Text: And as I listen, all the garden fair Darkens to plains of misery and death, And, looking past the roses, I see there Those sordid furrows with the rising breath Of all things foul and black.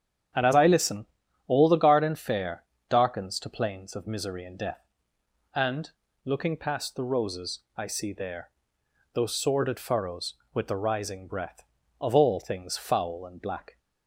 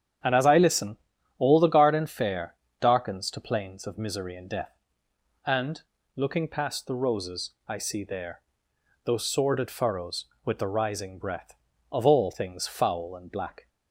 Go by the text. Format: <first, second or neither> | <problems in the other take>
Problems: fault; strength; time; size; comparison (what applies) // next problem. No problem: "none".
neither | starts louder than the rest; strong; the same in both // pauses between "fair" and "Darkens"; slight; the same in both // pauses between "there" and "Those"; noticeable; the same in both